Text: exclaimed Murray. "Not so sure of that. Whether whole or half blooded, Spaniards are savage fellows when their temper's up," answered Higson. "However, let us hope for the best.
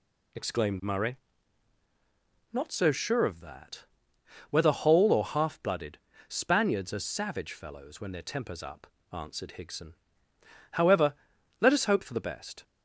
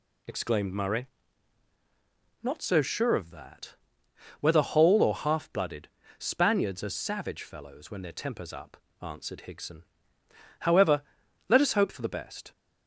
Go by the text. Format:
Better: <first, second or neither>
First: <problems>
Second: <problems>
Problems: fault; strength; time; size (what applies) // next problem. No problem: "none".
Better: neither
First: none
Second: none